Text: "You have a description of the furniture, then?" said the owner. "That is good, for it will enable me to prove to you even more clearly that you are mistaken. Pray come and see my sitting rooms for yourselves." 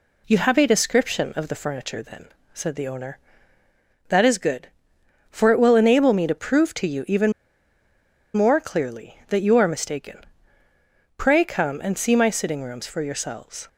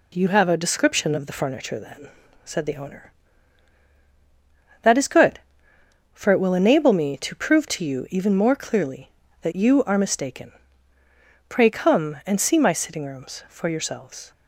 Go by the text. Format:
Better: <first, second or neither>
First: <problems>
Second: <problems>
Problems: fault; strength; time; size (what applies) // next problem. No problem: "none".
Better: second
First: pauses between "even" and "more"; at 7.3 s; 1.0 s long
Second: none